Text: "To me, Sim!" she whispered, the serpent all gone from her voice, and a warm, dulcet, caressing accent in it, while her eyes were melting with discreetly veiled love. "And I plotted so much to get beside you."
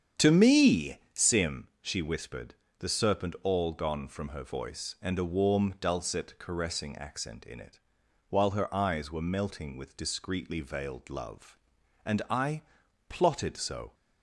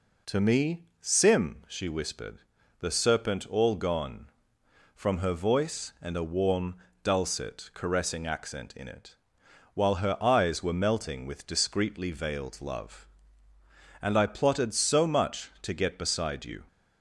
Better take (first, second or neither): second